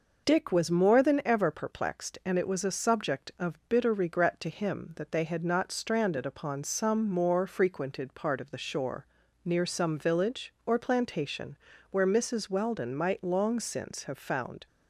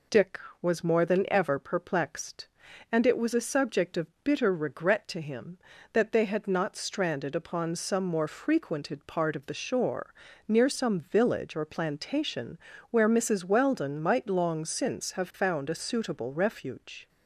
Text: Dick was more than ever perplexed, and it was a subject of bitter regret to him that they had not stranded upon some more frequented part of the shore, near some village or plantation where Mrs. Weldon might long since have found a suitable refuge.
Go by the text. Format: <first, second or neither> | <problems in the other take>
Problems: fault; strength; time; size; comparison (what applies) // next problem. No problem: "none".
second | pauses between "plantation" and "where"; slight; at 11.5 s; 0.32 s long; slight in the second // stops before "a suitable refuge"; at 14.6 s